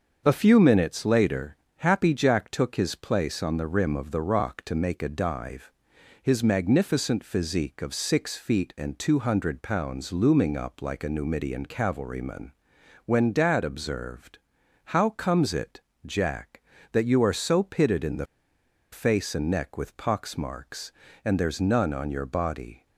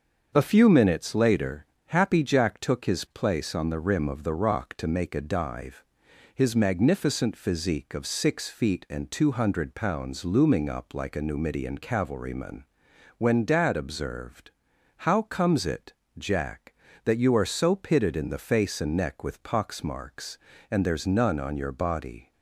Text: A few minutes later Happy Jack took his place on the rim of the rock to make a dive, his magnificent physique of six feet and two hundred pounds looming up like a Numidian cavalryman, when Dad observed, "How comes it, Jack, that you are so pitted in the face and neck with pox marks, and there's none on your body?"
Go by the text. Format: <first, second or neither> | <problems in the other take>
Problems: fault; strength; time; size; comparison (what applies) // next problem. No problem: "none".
second | starts louder than the rest; until 1.2 s; 7 dB; also in the second // pauses between "later" and "Happy"; slight; at 1.5 s; 0.22 s long; slight in the second // pauses between "the" and "face"; noticeable; at 18.2 s; 0.66 s long